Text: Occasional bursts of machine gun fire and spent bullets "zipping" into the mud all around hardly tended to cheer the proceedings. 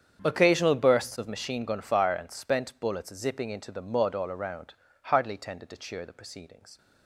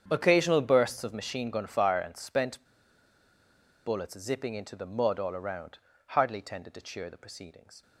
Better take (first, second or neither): first